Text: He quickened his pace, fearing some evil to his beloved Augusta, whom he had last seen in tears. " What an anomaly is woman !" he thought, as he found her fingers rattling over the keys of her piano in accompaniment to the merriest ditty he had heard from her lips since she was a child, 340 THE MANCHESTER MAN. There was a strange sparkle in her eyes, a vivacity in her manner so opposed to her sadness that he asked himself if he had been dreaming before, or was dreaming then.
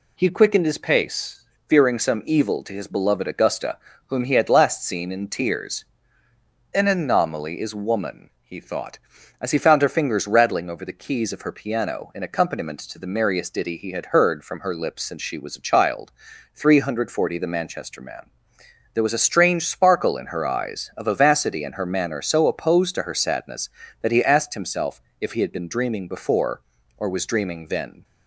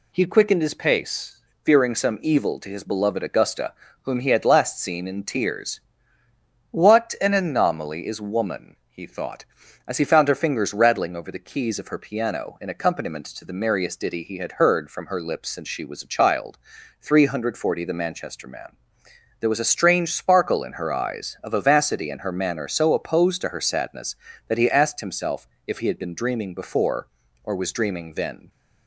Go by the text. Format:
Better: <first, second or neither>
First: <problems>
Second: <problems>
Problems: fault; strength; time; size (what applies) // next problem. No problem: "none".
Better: second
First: skips "What"; at 6.7 s // pauses between "himself" and "if"; slight; at 25.0 s; 0.18 s long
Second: pauses between "himself" and "if"; slight; at 25.4 s; 0.18 s long